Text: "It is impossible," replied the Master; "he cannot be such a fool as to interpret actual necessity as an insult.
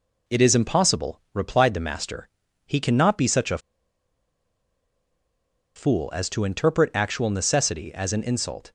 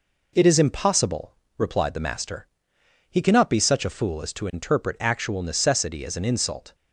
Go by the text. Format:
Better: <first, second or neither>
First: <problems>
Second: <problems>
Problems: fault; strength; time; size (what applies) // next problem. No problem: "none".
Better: second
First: pauses between "a" and "fool"; strong; at 3.5 s; 2.1 s long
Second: none